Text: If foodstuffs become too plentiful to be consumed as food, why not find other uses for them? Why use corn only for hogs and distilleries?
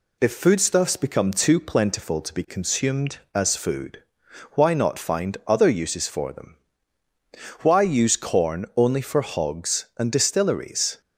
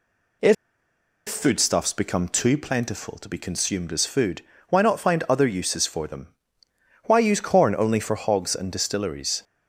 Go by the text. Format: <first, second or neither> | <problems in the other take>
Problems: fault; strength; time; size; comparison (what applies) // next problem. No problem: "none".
first | pauses between "If" and "foodstuffs"; noticeable; at 0.5 s; 0.72 s long